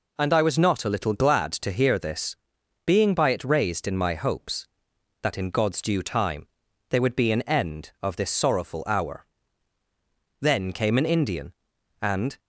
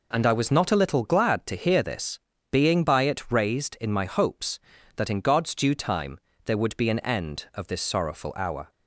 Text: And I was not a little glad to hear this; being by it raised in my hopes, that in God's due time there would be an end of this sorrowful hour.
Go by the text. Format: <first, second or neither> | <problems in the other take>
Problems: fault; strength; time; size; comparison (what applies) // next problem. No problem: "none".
second | pauses between "time" and "there"; at 6.4 s; 0.42 s long; slight in the second // goes on to say "Then came an Indian and"; strong; from 10.4 s on; 1.9 s long